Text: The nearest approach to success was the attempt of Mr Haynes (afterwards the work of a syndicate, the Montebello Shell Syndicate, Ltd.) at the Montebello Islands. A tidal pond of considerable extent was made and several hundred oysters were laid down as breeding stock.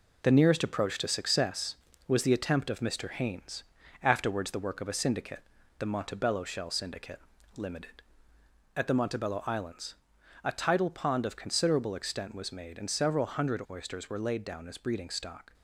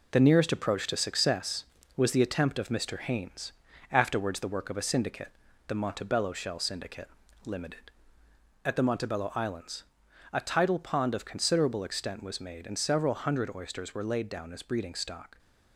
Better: neither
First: none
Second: none

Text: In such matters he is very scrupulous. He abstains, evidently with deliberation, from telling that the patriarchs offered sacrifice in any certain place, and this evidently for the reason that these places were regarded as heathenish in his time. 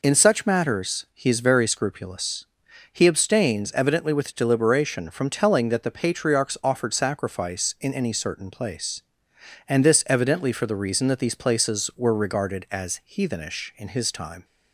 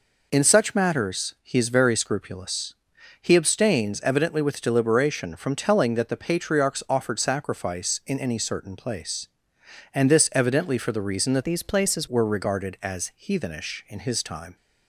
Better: first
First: none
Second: changes voice from "these" to "places"; from 11.4 to 12.0 s; 0.6 s long

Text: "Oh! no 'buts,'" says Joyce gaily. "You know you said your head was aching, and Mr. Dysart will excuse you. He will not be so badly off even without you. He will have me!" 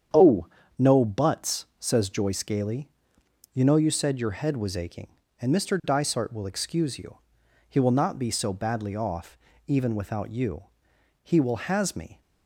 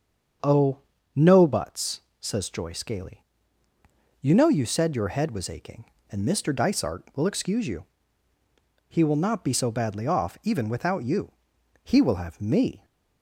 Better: second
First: starts louder than the rest; strong; until 1.4 s; 8 dB // pauses between "off" and "even"; slight; at 9.3 s; 0.30 s long // says "has" for "have"; at 11.5 s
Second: starts louder than the rest; until 1.7 s; 7 dB

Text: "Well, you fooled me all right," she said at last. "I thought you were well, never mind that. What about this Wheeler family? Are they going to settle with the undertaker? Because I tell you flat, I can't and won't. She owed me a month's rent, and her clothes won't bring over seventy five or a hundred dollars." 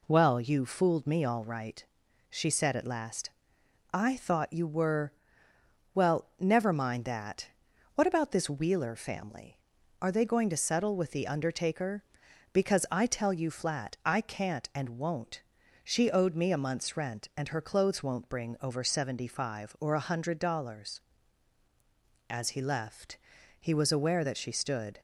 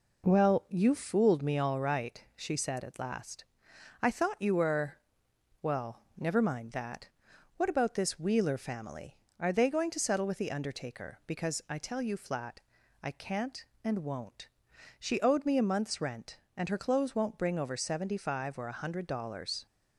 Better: second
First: pauses between "were" and "well"; noticeable; at 5.1 s; 0.80 s long // goes on to say "As he left he was aware that she stood"; strong; from 22.2 s on; 2.7 s long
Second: pauses between "were" and "well"; noticeable; at 4.9 s; 0.64 s long

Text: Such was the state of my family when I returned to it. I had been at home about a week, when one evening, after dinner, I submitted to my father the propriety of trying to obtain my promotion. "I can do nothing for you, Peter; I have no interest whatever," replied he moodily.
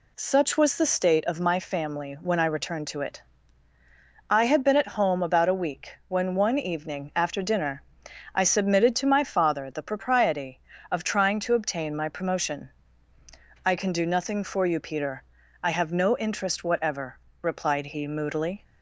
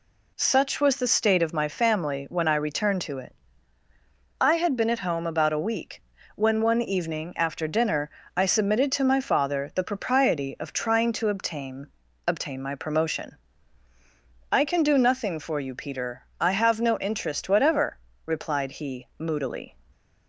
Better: first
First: none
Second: says "obtain" twice; at 12.2 s

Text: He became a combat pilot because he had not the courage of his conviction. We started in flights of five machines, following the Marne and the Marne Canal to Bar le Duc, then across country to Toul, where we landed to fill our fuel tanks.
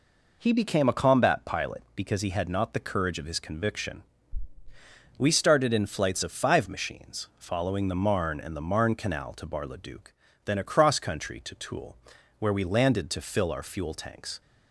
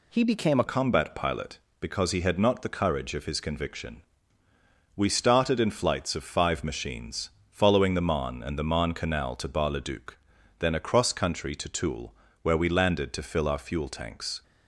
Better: first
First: none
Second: changes voice at "combat"; from 0.6 s on; 13.8 s long

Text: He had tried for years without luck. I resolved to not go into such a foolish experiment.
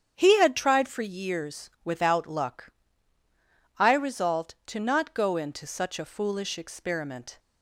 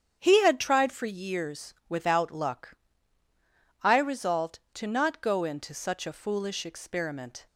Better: neither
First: starts louder than the rest; strong; until 1.1 s; 8.5 dB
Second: starts louder than the rest; strong; until 1.2 s; 8.5 dB

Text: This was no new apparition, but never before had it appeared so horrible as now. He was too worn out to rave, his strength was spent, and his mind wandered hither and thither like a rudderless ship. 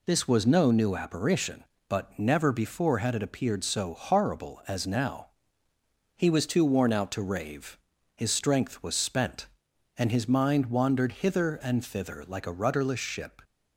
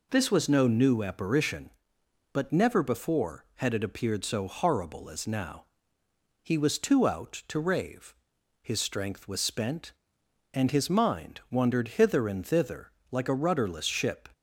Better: first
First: none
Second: skips "worn"; at 7.0 s // pauses between "thither" and "like"; slight; at 12.9 s; 0.20 s long

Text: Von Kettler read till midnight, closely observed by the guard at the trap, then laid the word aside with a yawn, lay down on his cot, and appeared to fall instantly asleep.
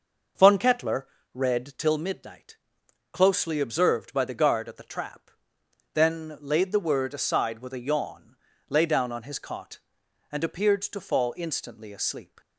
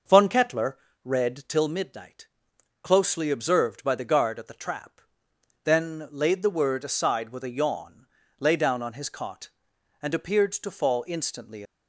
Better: first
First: pauses between "Kettler" and "read"; slight; at 1.0 s; 0.26 s long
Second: pauses between "Kettler" and "read"; slight; at 0.7 s; 0.26 s long // stops before "asleep"; at 11.6 s

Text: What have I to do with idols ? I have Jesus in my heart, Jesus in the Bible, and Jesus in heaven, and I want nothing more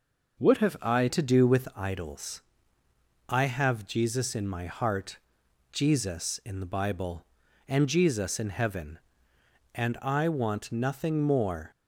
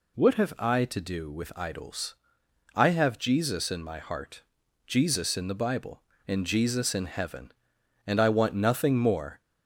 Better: second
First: changes voice at "to"; from 1.0 s on; 10.7 s long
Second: none

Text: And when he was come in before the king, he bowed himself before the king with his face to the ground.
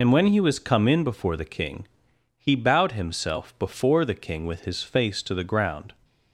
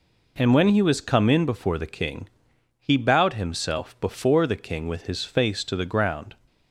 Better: second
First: loses the start of "And"; at 0.0 s; 60 ms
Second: none

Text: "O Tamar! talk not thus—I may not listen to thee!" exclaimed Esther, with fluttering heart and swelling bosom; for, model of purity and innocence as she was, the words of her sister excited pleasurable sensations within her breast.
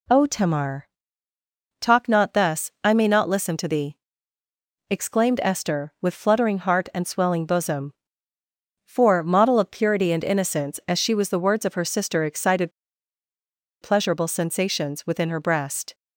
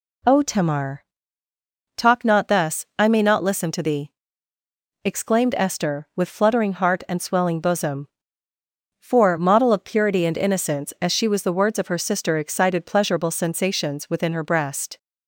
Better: second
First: pauses between "excited" and "pleasurable"; at 12.7 s; 1.1 s long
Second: none

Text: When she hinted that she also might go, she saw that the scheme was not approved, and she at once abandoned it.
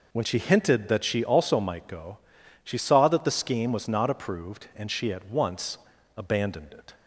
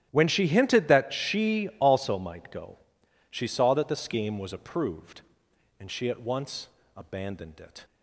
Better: first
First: pauses between "once" and "abandoned"; at 5.7 s; 0.38 s long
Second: starts louder than the rest; strong; until 1.1 s; 11.5 dB // skips "not"; at 4.5 s // pauses between "once" and "abandoned"; slight; at 6.6 s; 0.28 s long

